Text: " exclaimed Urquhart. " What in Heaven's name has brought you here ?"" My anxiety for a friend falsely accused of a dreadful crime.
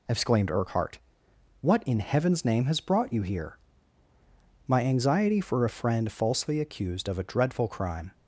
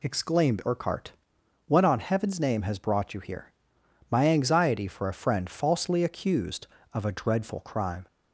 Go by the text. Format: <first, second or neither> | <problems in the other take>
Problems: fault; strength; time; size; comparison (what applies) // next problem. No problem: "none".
first | says "on" for "in"; at 1.8 s